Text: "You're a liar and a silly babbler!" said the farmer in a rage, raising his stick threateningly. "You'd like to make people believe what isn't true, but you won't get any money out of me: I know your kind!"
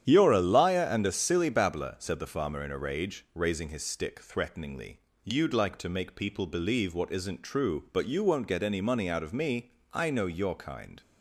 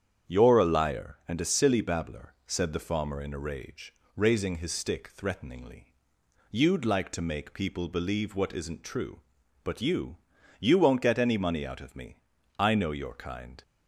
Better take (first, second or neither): first